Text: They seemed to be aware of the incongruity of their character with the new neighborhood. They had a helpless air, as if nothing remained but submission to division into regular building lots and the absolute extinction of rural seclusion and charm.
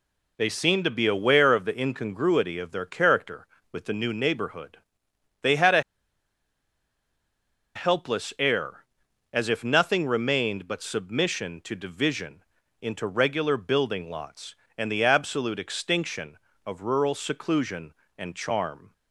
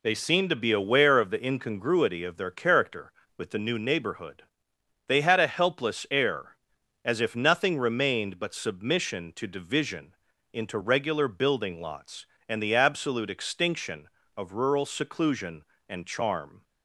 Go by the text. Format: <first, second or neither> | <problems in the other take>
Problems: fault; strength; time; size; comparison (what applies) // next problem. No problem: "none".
second | pauses between "a" and "helpless"; strong; at 5.8 s; 1.9 s long // pauses between "division" and "into"; at 12.4 s; 0.38 s long; also in the second